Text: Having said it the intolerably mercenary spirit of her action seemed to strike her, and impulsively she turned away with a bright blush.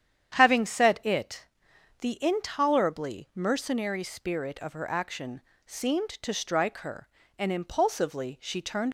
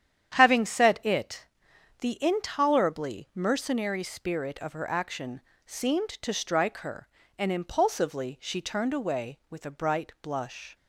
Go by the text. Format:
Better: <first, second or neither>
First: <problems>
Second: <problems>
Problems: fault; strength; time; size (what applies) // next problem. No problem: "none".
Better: second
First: starts louder than the rest; strong; until 1.3 s; 9 dB // pauses between "it" and "the"; noticeable; at 1.4 s; 0.56 s long // pauses between "action" and "seemed"; slight; at 5.4 s; 0.26 s long // stops before "away with a bright blush"; at 8.8 s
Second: starts louder than the rest; strong; until 1.3 s; 9.5 dB // pauses between "it" and "the"; noticeable; at 1.4 s; 0.56 s long // pauses between "action" and "seemed"; slight; at 5.4 s; 0.26 s long